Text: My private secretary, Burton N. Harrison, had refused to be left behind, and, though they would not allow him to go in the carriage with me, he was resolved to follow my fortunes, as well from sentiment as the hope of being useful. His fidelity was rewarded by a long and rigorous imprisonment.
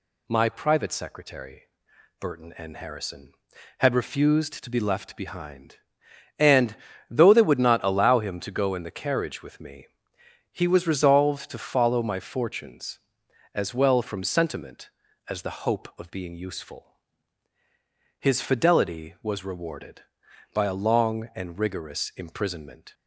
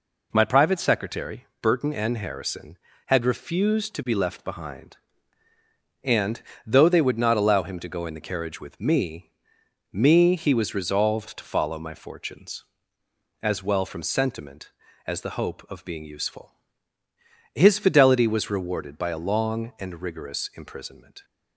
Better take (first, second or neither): first